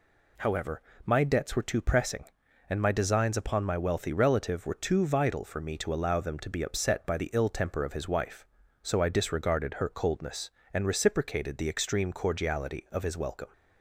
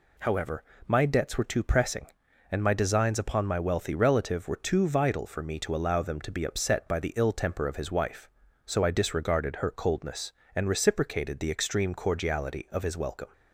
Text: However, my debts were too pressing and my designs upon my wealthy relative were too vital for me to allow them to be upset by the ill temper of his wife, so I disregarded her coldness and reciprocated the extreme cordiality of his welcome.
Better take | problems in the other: neither | none

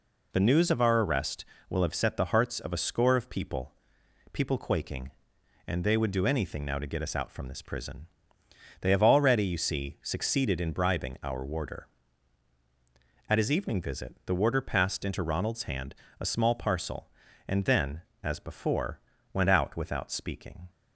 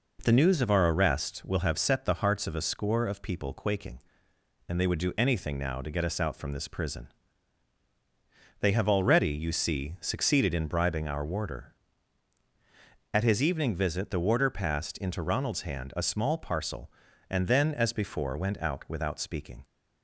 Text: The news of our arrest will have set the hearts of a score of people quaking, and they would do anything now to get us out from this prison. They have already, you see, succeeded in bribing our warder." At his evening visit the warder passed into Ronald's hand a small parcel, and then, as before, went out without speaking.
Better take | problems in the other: second | says "people" twice; at 4.3 s // pauses between "hand" and "a"; slight; at 15.9 s; 0.26 s long

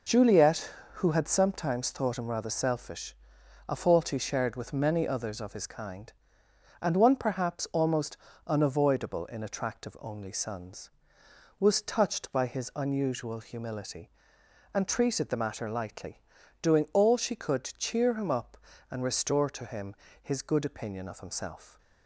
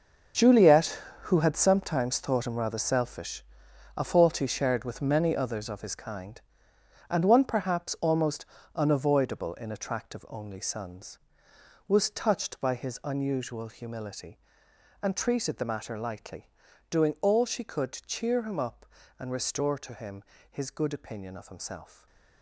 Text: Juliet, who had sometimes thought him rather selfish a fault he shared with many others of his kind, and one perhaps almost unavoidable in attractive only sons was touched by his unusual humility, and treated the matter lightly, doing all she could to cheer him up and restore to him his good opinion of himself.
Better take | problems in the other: first | gets quieter; strong; throughout; 12.5 dB // pauses between "selfish" and "a"; noticeable; at 3.4 s; 0.54 s long; noticeable in the first // pauses between "almost" and "unavoidable"; slight; at 8.4 s; 0.30 s long; slight in the first // pauses between "him" and "his"; slight; at 20.2 s; 0.28 s long; slight in the first // stays silent after the last word; slight; from 21.9 s on; 0.5 s long

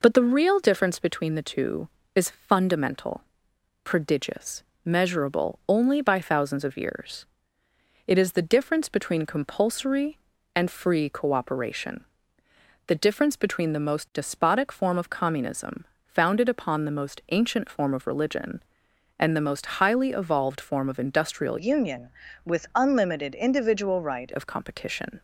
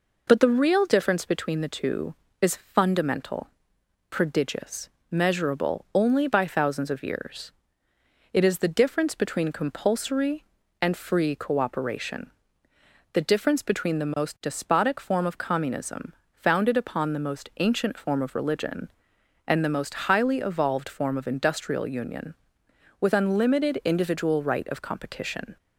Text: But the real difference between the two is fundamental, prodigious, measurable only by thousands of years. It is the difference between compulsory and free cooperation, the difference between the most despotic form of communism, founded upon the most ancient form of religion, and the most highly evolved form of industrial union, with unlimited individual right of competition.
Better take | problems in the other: second | changes voice from "union" to "right"; from 21.5 to 24.2 s; 2.7 s long

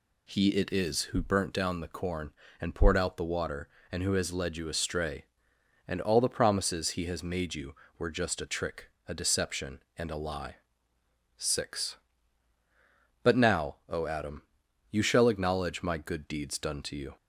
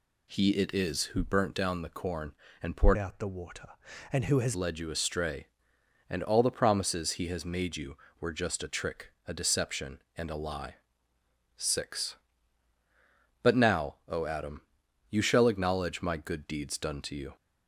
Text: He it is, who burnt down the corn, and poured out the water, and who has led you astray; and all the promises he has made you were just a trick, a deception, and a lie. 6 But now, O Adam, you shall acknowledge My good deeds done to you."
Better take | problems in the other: first | changes voice from "out" to "has"; from 2.9 to 4.5 s; 1.6 s long

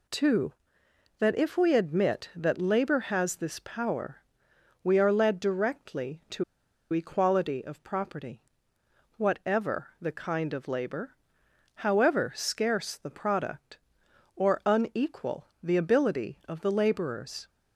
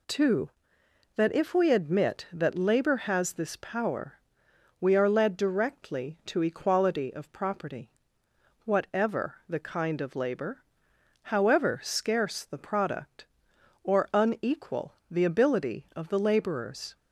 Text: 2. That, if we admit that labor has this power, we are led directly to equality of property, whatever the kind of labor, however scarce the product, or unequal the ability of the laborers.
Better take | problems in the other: second | pauses between "to" and "equality"; noticeable; at 6.4 s; 0.48 s long

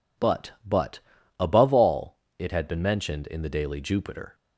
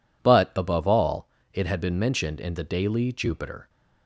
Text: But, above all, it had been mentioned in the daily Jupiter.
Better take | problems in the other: second | says "But" twice; at 0.6 s

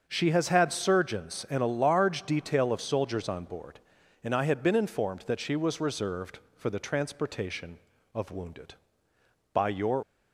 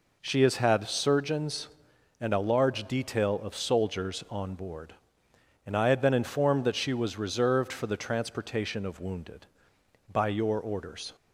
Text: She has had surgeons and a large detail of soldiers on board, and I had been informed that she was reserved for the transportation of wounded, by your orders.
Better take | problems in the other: second | starts louder than the rest; until 1.0 s; 6.5 dB // stops before "orders"; at 10.0 s

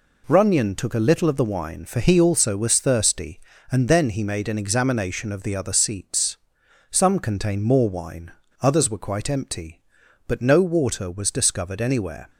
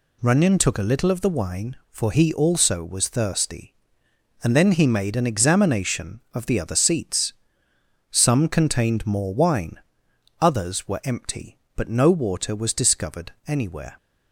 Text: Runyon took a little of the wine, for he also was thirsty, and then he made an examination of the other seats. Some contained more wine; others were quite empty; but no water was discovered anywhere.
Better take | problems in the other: first | skips "quite"; at 11.0 s

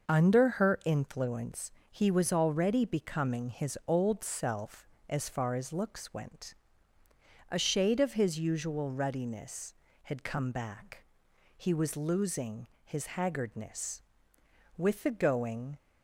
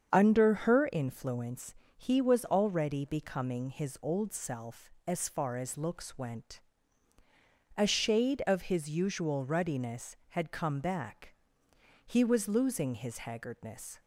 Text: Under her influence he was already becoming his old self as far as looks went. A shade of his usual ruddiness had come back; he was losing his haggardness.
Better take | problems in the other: second | starts louder than the rest; noticeable; until 1.1 s; 6 dB; strong in the second // pauses between "influence" and "he"; slight; at 1.7 s; 0.18 s long; slight in the second // pauses between "losing" and "his"; slight; at 12.6 s; 0.16 s long // goes on to say "With the going"; noticeable; from 14.7 s on; 1.0 s long

